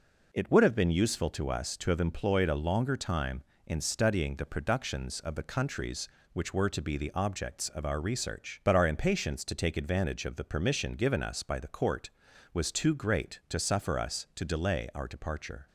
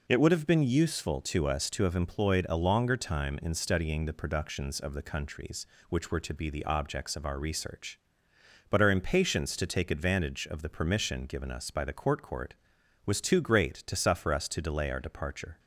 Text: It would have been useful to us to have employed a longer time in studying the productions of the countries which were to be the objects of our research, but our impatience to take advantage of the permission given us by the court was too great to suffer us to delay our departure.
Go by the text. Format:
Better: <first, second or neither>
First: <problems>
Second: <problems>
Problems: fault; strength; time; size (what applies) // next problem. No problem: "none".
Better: first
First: none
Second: says "court" twice; at 12.2 s